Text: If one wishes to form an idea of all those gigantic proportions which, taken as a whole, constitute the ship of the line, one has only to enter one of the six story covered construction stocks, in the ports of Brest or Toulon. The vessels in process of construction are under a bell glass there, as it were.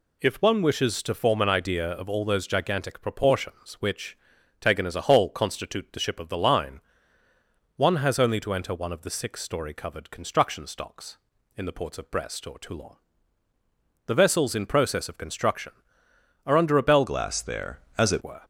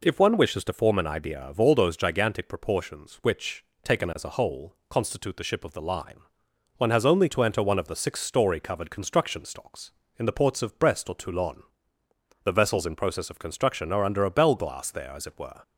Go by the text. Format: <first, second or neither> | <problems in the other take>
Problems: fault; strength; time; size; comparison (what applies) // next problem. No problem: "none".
second | changes voice from "glass" to "it"; from 17.0 to 18.2 s; 1.2 s long